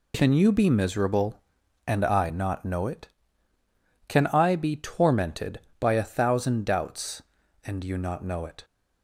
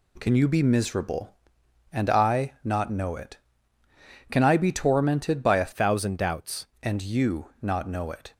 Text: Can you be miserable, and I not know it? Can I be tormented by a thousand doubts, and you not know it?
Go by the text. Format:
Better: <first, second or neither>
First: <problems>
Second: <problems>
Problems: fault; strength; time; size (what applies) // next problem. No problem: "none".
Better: first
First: none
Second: changes voice from "thousand" to "doubts"; from 5.7 to 6.6 s; 0.9 s long